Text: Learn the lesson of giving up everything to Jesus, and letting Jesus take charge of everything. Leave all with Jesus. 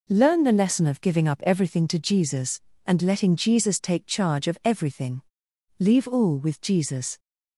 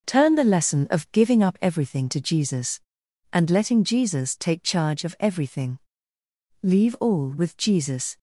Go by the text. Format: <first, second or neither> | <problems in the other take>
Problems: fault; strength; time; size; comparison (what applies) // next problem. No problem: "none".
first | says "Turn" for "Learn"; at 0.0 s